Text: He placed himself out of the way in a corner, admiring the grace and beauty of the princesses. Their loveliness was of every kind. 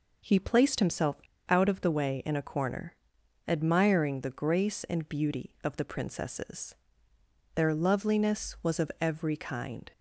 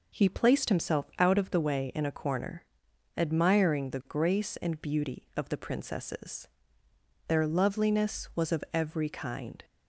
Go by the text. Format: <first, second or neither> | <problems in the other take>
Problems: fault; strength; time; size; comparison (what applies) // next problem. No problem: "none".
second | pauses between "himself" and "out"; slight; at 1.1 s; 0.28 s long